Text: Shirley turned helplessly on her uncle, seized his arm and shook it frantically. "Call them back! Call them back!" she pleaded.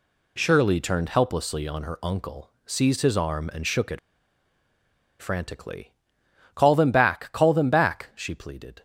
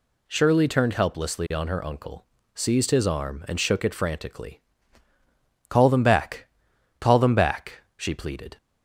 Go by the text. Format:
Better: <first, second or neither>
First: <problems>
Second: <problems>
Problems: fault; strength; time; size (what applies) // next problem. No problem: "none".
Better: second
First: pauses between "it" and "frantically"; at 3.9 s; 1.2 s long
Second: none